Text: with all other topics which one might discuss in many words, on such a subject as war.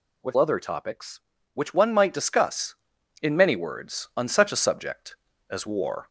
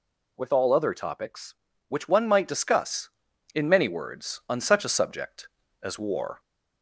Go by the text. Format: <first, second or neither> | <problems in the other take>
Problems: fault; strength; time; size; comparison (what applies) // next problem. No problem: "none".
second | skips "all"; at 0.3 s